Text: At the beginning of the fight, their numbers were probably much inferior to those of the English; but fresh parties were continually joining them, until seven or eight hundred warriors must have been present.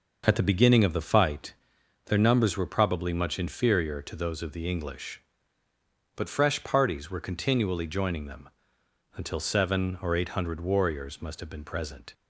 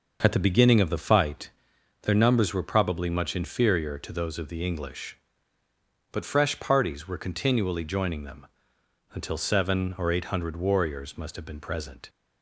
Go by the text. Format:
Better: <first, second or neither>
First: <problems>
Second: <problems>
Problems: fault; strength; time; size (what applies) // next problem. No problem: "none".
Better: neither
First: none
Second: none